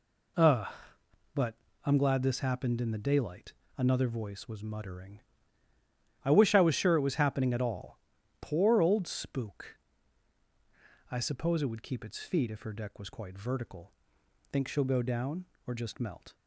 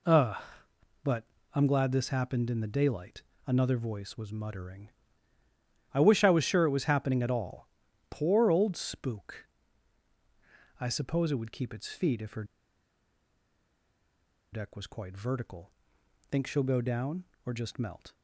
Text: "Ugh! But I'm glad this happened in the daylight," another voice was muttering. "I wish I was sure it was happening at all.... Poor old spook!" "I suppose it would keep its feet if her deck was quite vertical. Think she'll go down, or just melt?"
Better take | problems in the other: first | pauses between "But" and "I'm"; slight; at 1.2 s; 0.30 s long; slight in the first // pauses between "her" and "deck"; strong; at 12.4 s; 2.0 s long

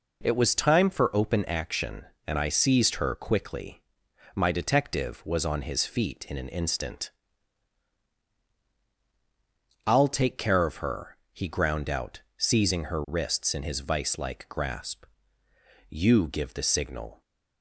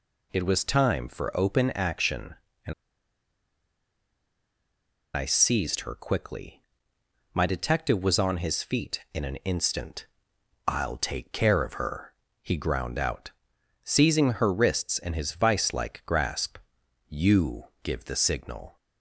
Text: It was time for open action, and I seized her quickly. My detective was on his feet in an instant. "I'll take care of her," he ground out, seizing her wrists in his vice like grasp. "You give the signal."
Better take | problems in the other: first | pauses between "and" and "I"; strong; at 2.7 s; 2.4 s long // pauses between "You" and "give"; slight; at 17.6 s; 0.18 s long

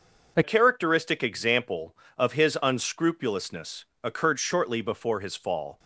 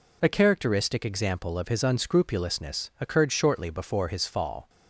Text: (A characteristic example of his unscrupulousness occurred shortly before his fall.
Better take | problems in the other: second | changes voice at "characteristic"; from 0.4 s on; 5.3 s long // pauses between "unscrupulousness" and "occurred"; slight; at 3.8 s; 0.18 s long

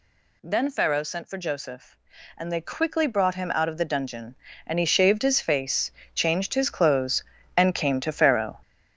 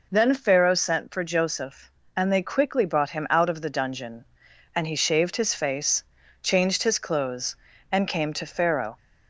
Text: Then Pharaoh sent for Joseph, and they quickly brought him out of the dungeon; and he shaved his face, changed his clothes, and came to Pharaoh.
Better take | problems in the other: second | gets louder; strong; throughout; 8 dB

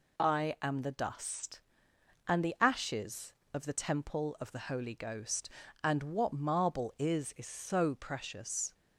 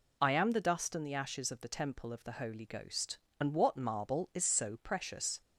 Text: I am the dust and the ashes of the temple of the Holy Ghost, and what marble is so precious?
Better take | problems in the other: second | says "is" twice; at 7.3 s

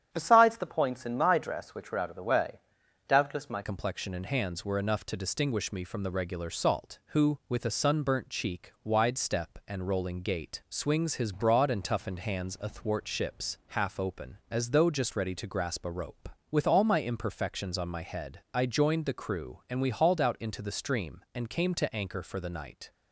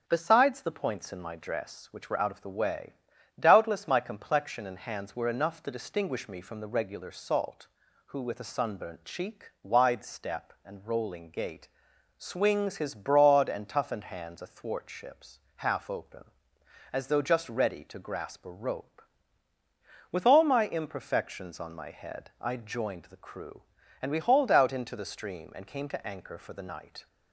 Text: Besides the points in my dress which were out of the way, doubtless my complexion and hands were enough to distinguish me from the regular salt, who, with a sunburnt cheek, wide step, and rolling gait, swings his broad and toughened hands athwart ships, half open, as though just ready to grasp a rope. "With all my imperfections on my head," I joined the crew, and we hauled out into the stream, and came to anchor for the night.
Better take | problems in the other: second | starts louder than the rest; strong; until 1.1 s; 9.5 dB; strong in the second // changes voice at "complexion"; from 3.6 s on; 19.3 s long

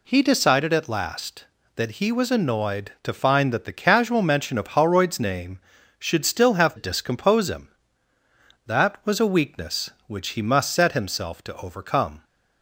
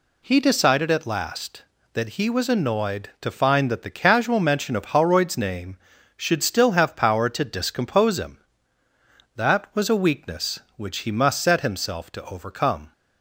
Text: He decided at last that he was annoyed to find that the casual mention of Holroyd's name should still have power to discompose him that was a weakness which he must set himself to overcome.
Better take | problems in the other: second | skips "power to"; at 6.7 s

